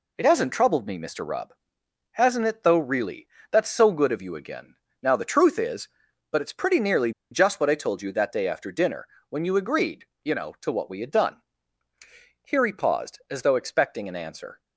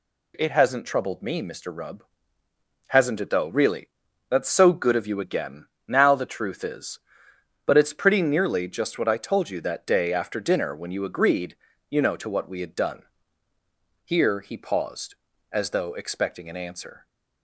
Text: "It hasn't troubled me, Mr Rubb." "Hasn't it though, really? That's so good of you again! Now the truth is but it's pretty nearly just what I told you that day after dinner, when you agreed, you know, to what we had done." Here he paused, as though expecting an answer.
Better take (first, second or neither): second